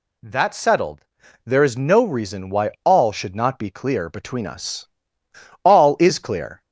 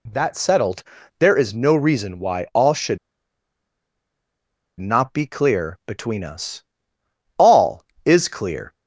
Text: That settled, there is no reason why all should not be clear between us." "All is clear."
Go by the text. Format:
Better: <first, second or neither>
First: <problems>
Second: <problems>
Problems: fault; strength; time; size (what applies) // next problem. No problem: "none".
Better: first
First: none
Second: pauses between "should" and "not"; strong; at 2.9 s; 1.8 s long